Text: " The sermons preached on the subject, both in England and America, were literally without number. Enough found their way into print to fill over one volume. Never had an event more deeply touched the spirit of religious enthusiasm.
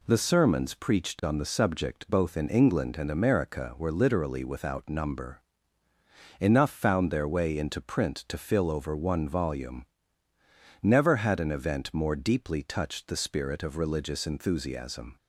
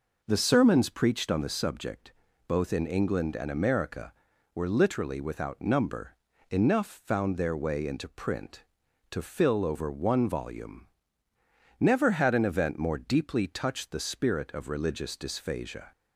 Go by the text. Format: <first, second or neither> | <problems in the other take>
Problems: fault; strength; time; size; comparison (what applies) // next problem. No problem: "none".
first | says "dysphagia" for "enthusiasm"; at 15.1 s